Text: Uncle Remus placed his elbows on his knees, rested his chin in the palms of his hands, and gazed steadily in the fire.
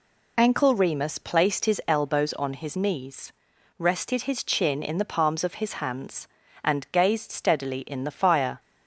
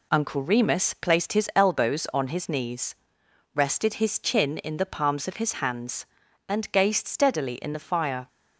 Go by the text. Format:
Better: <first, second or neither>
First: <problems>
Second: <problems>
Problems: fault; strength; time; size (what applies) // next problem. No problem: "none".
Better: second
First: says "Ankle" for "Uncle"; at 0.3 s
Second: none